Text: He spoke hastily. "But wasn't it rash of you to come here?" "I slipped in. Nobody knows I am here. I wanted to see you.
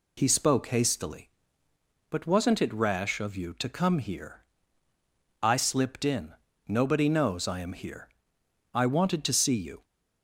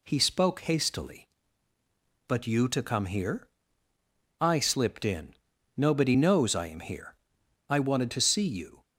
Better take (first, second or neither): first